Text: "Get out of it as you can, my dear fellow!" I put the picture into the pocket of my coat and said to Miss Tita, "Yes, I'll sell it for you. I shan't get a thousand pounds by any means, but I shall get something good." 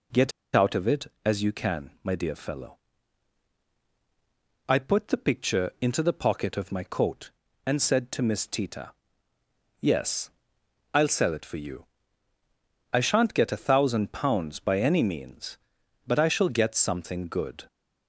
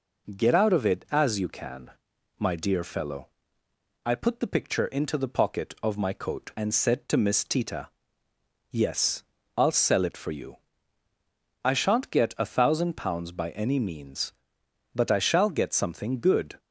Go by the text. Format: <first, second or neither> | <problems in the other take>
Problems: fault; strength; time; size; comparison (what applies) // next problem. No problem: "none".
second | pauses between "Get" and "out"; slight; at 0.3 s; 0.23 s long